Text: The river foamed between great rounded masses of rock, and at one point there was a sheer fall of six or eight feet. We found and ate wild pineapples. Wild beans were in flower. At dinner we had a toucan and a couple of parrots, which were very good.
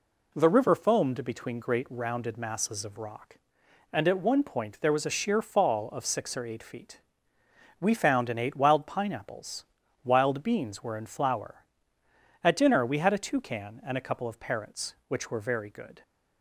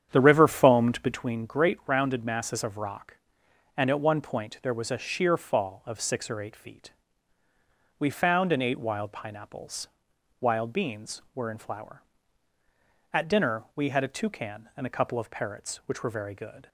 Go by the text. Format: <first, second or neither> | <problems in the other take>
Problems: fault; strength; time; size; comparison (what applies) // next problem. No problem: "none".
first | starts louder than the rest; strong; until 1.3 s; 9 dB